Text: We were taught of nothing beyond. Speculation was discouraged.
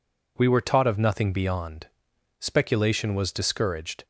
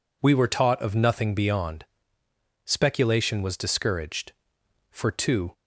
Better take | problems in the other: first | goes on to say "For two"; noticeable; from 4.9 s on; 0.62 s long

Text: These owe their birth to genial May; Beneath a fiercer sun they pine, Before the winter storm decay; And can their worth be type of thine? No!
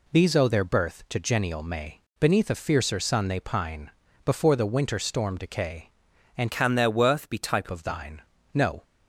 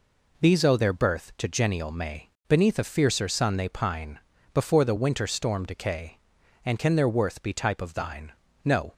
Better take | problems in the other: second | changes voice from "can" to "type"; from 6.5 to 7.6 s; 1.1 s long

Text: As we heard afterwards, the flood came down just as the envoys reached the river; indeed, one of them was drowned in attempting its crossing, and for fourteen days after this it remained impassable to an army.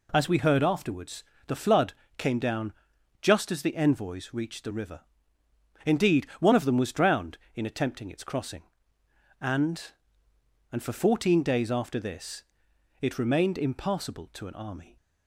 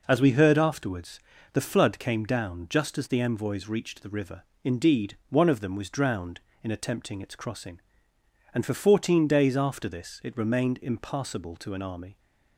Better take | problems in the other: second | pauses between "flood" and "came"; slight; at 1.9 s; 0.24 s long // pauses between "down" and "just"; noticeable; at 2.7 s; 0.50 s long // says "and" twice; at 10.7 s // pauses between "this" and "it"; noticeable; at 12.4 s; 0.60 s long

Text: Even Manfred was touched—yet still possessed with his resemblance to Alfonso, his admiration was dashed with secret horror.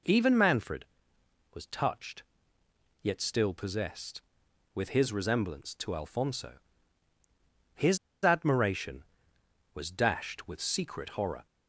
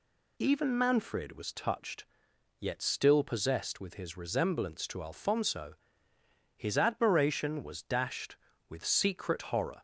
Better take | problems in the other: second | pauses between "his" and "admiration"; slight; at 7.9 s; 0.25 s long

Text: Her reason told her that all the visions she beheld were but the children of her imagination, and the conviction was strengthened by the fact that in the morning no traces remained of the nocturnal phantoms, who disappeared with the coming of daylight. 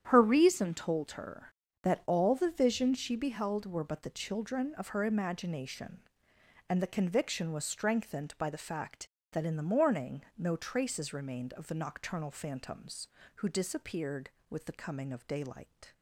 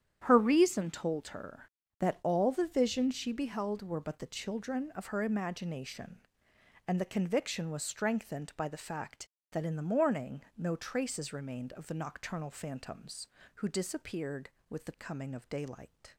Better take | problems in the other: neither | starts louder than the rest; strong; the same in both // pauses between "morning" and "no"; slight; the same in both

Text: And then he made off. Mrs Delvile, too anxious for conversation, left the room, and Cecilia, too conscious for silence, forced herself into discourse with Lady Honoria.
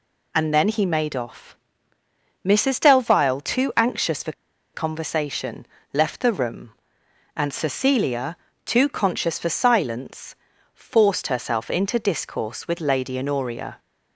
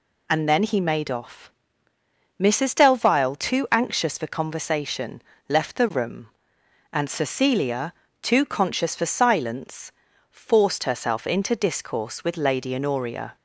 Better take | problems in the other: second | pauses between "for" and "conversation"; at 4.3 s; 0.42 s long

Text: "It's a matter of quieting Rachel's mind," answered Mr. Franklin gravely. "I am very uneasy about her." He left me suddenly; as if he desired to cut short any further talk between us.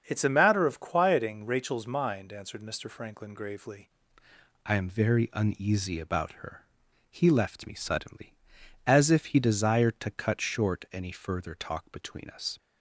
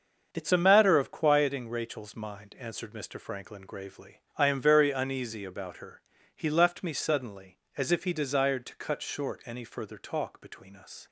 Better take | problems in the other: second | starts louder than the rest; until 1.0 s; 6.5 dB; also in the second // changes voice at "I"; from 4.6 s on; 7.9 s long

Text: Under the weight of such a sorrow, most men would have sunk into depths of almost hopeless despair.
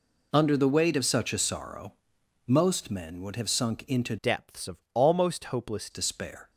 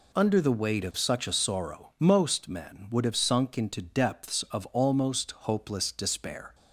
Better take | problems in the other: second | changes voice from "depths" to "hopeless"; from 4.2 to 5.8 s; 1.6 s long

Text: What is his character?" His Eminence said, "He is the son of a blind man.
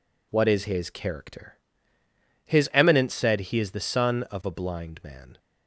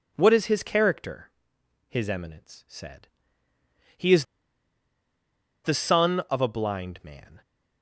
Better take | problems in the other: first | pauses between "is" and "the"; strong; at 4.2 s; 1.3 s long

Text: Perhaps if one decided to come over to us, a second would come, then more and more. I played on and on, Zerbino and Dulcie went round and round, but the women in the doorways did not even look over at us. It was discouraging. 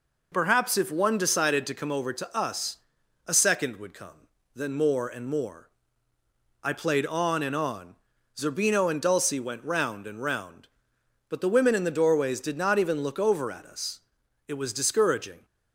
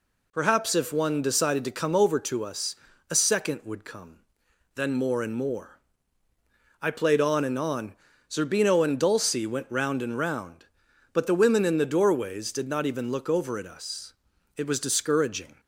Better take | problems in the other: neither | none

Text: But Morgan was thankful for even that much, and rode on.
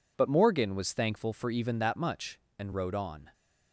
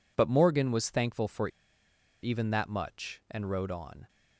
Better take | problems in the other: first | pauses between "for" and "even"; noticeable; at 1.4 s; 0.75 s long

